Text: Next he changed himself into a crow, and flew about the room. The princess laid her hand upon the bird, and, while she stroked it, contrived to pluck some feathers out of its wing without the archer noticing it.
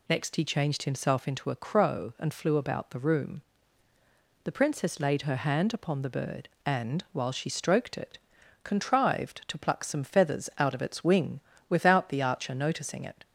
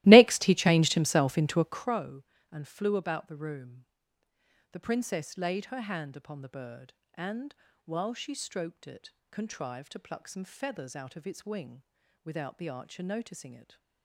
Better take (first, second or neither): first